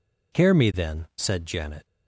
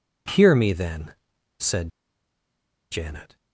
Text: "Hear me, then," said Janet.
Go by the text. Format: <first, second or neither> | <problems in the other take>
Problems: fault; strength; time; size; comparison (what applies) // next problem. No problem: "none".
first | pauses between "said" and "Janet"; at 1.8 s; 1.0 s long